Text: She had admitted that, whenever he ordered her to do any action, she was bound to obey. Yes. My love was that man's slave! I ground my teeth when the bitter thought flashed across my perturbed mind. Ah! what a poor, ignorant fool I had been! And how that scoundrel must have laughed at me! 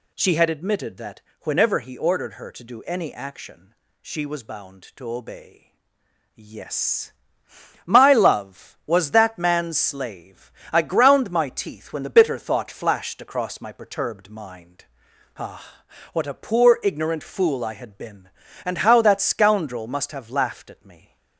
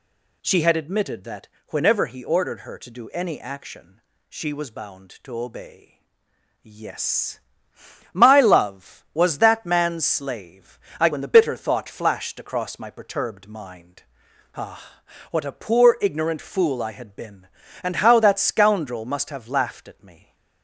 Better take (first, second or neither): first